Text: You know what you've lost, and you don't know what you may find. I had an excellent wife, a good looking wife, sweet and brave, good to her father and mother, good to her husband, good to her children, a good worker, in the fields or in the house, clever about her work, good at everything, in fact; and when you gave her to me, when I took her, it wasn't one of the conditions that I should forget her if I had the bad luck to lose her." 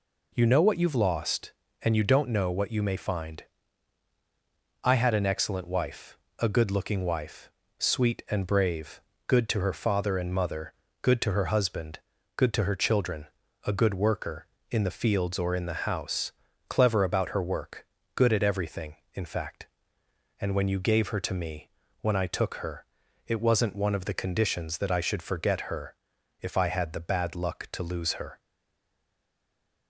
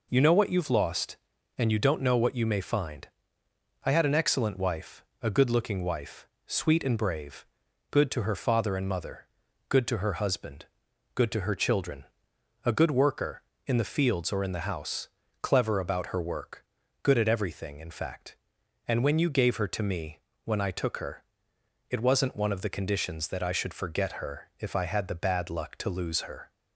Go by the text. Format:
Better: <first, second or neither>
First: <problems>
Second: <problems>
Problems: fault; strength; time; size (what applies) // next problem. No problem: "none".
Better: second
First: pauses between "her" and "if"; noticeable; at 25.9 s; 0.48 s long // stays silent after the last word; noticeable; from 28.3 s on; 1.5 s long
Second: none